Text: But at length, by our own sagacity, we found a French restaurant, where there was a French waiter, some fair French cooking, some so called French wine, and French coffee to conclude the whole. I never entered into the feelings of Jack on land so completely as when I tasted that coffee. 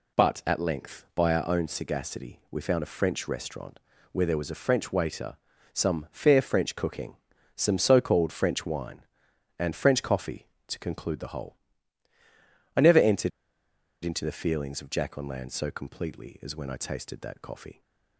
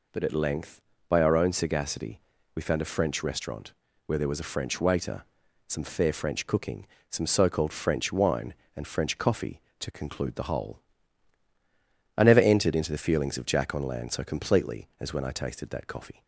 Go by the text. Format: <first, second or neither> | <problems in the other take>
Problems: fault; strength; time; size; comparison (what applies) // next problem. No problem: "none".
second | pauses between "entered" and "into"; noticeable; at 13.3 s; 0.74 s long